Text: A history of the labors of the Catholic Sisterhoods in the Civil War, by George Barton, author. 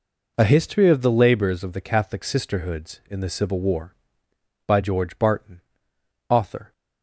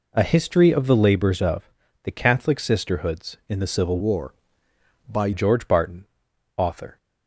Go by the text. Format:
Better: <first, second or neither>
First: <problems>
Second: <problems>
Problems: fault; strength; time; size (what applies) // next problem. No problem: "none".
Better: first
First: none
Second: pauses between "of" and "the"; slight; at 1.6 s; 0.36 s long // changes voice from "War" to "by"; from 3.9 to 5.3 s; 1.4 s long